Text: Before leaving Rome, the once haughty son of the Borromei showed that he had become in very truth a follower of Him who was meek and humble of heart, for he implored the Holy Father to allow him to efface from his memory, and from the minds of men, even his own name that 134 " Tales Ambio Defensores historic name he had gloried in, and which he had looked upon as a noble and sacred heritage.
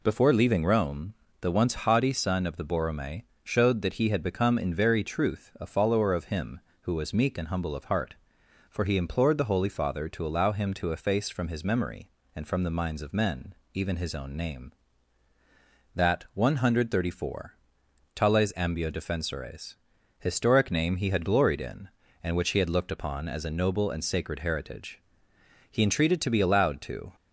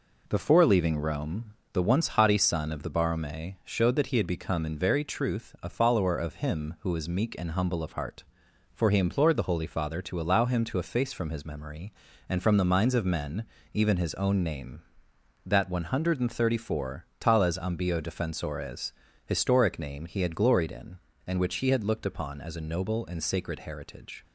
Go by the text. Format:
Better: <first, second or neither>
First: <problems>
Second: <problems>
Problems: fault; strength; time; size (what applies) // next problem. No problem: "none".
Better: second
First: pauses between "Borromei" and "showed"; slight; at 3.2 s; 0.22 s long // pauses between "Defensores" and "historic"; at 19.7 s; 0.42 s long // goes on to say "He entreated to be allowed to"; from 25.6 s on; 1.4 s long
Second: pauses between "Defensores" and "historic"; slight; at 18.9 s; 0.32 s long